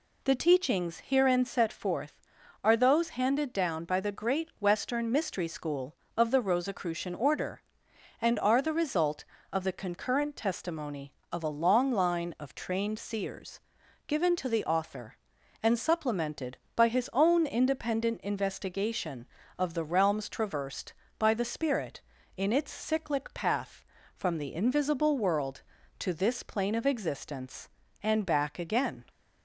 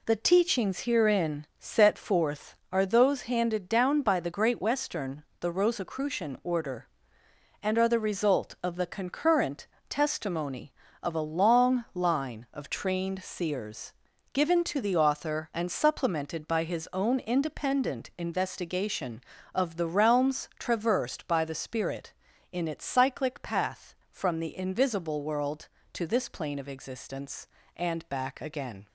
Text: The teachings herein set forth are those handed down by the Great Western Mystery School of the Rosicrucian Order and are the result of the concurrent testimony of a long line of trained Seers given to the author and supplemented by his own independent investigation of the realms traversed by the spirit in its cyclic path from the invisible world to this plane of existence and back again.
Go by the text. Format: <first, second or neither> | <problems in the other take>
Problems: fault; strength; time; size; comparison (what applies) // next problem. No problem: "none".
first | skips "Mystery School of"; at 5.3 s // pauses between "concurrent" and "testimony"; slight; at 9.6 s; 0.22 s long // pauses between "Seers" and "given"; at 13.9 s; 0.40 s long; noticeable in the first